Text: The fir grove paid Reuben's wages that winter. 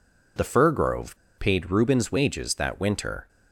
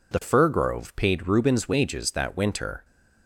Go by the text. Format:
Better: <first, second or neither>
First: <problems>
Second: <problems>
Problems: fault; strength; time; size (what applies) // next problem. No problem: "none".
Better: second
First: pauses between "grove" and "paid"; slight; at 1.1 s; 0.20 s long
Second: none